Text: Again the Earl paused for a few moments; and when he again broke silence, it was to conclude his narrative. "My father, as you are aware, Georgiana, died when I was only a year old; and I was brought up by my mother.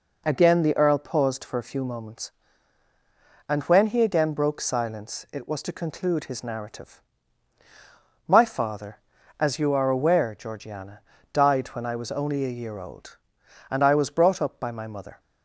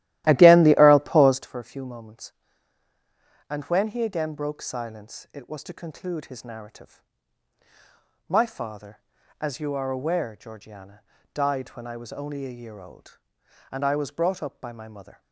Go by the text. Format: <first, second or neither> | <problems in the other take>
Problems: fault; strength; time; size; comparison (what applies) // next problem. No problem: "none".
first | starts louder than the rest; strong; until 1.5 s; 14.5 dB